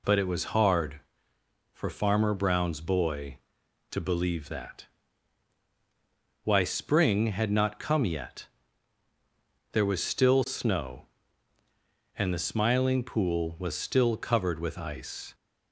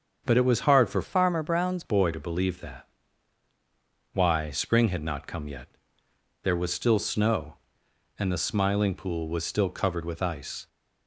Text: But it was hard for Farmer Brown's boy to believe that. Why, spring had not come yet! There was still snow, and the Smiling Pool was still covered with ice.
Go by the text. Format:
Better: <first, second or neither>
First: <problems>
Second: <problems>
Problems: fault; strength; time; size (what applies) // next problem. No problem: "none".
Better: first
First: none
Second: starts louder than the rest; until 1.2 s; 6.5 dB // changes voice from "Farmer" to "Brown's"; from 1.0 to 1.8 s; 0.8 s long